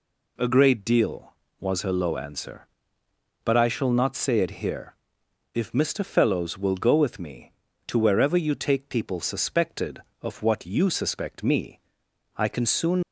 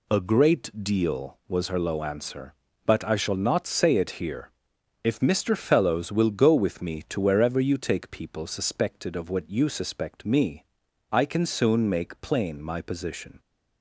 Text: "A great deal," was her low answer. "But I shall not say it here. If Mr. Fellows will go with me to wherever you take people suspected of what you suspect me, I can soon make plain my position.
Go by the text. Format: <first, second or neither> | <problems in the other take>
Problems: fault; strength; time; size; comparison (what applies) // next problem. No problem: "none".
second | stops before "make plain my position"; at 13.0 s